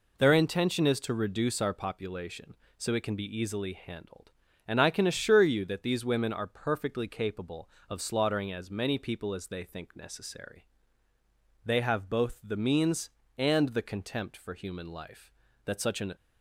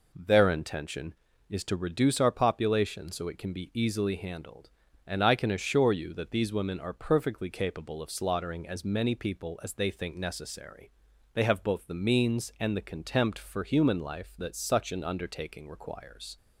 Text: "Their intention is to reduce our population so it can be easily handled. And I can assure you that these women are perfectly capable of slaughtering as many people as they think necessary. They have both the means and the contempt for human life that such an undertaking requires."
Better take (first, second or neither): second